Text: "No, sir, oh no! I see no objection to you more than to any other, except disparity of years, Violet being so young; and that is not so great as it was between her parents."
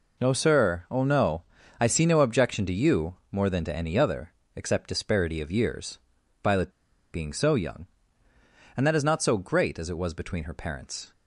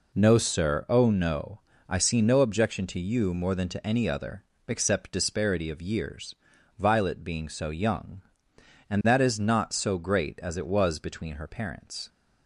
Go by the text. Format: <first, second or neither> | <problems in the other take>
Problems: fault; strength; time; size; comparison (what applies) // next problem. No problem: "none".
second | pauses between "you" and "more"; slight; at 3.1 s; 0.16 s long // pauses between "Violet" and "being"; at 6.6 s; 0.43 s long